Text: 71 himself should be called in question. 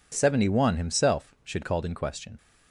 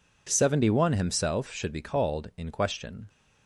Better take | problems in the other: second | skips "be"; at 1.6 s

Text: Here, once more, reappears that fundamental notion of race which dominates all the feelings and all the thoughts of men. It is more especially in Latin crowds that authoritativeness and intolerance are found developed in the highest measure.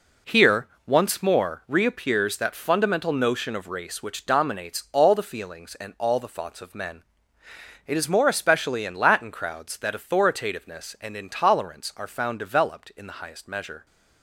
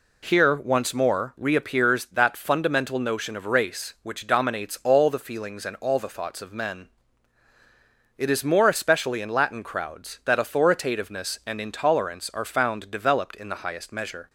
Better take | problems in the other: second | gets quieter; strong; throughout; 9.5 dB

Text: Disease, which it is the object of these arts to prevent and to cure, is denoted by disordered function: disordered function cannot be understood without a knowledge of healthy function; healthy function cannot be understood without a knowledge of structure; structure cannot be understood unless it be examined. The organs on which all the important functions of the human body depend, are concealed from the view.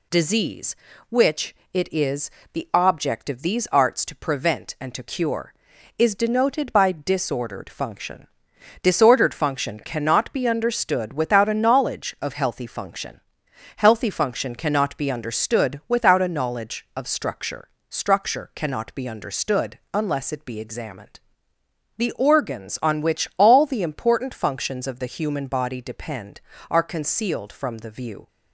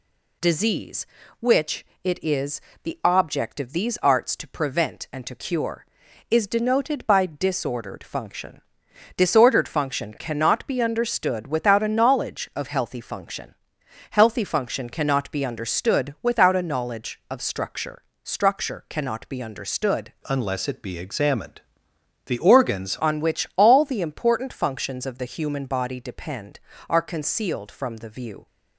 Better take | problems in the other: first | pauses between "which" and "it"; slight; at 1.8 s; 0.18 s long; slight in the first // pauses between "is" and "the"; slight; at 2.6 s; 0.22 s long; slight in the first // changes voice from "unless" to "organs"; from 20.2 to 22.9 s; 2.7 s long

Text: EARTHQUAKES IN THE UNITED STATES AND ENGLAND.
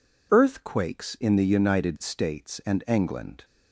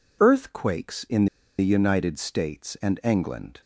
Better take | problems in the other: first | pauses between "IN" and "THE"; slight; at 1.2 s; 0.32 s long

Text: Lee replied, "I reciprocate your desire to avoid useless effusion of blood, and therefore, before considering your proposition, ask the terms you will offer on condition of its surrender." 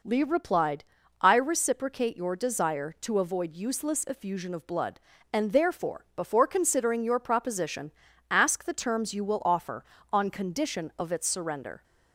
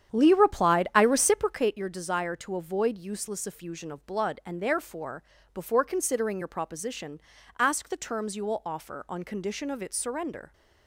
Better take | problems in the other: first | starts louder than the rest; strong; until 1.7 s; 9 dB

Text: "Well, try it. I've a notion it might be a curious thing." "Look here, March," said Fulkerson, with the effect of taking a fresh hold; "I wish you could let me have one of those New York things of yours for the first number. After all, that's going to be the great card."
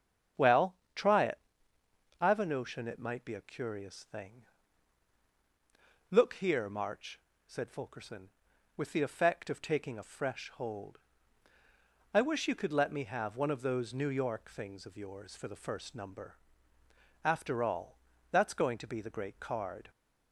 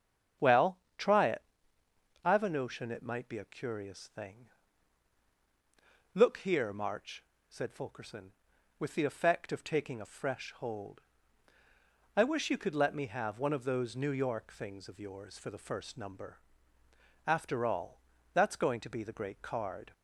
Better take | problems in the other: neither | starts louder than the rest; strong; the same in both

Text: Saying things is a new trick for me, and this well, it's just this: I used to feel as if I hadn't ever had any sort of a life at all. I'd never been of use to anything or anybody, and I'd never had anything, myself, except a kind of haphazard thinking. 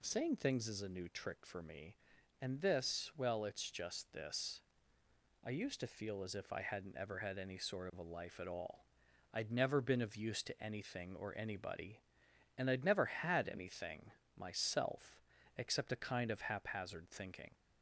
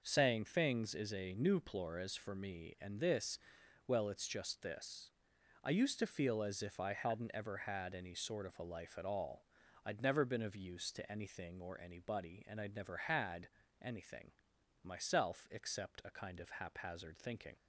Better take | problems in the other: first | says "plores" for "trick"; at 1.6 s // pauses between "this" and "well"; noticeable; at 3.3 s; 0.48 s long // pauses between "had" and "anything"; slight; at 13.4 s; 0.36 s long

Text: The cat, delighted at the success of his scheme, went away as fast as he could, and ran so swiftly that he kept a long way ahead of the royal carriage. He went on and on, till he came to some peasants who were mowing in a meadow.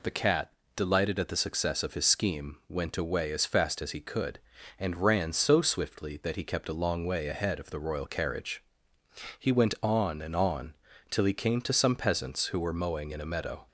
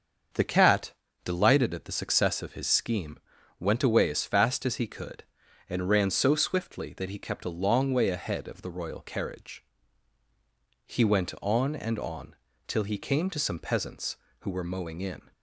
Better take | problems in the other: first | starts louder than the rest; until 1.6 s; 7 dB // stops before "a meadow"; at 15.3 s

